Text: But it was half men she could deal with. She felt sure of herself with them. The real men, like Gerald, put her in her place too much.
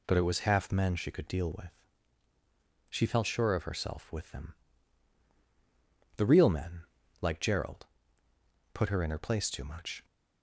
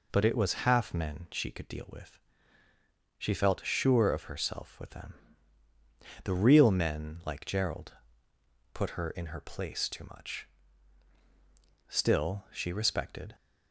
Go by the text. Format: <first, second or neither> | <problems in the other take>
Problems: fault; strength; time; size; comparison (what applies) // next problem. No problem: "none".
first | goes on to say "Still she respected"; from 11.8 s on; 1.4 s long